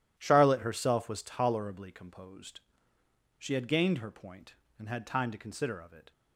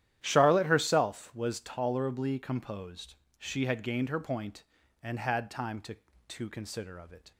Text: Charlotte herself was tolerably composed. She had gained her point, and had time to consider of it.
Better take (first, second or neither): first